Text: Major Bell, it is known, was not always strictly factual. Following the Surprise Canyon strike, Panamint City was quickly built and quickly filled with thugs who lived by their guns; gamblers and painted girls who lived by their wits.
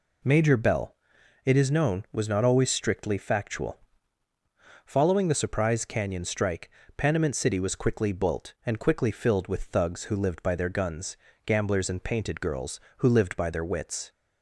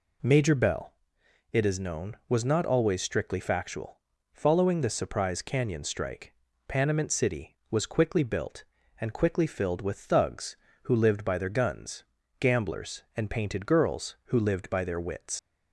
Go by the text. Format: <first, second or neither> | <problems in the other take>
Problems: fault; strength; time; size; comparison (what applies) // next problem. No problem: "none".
first | leaves "wits" unfinished; at 15.3 s; 110 ms